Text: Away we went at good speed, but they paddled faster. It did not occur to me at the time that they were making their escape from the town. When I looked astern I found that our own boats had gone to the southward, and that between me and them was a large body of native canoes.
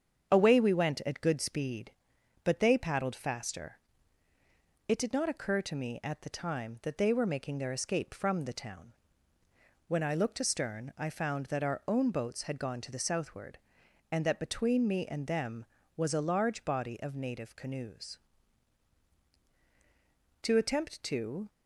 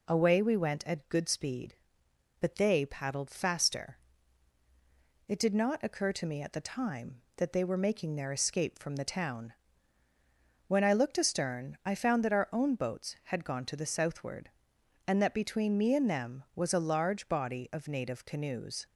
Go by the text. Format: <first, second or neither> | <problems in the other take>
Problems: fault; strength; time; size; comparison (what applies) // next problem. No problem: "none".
second | starts louder than the rest; strong; until 1.3 s; 8 dB // goes on to say "To attempt to"; noticeable; from 20.4 s on; 1.0 s long